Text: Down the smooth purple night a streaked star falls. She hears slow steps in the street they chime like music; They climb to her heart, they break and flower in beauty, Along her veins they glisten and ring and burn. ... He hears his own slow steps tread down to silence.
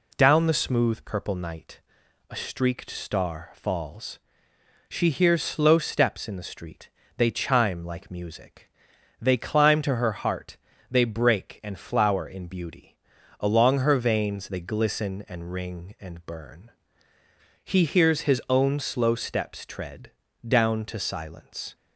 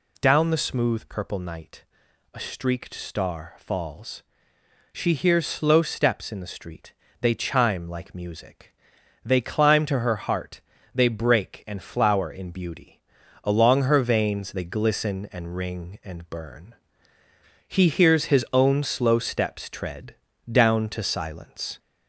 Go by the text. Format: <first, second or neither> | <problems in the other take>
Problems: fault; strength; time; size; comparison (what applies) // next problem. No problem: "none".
first | gets louder; slight; throughout; 2.5 dB // pauses between "night" and "a"; noticeable; at 1.8 s; 0.50 s long; noticeable in the first // pauses between "street" and "they"; slight; at 6.9 s; 0.26 s long; slight in the first // pauses between "tread" and "down"; slight; at 20.1 s; 0.36 s long; slight in the first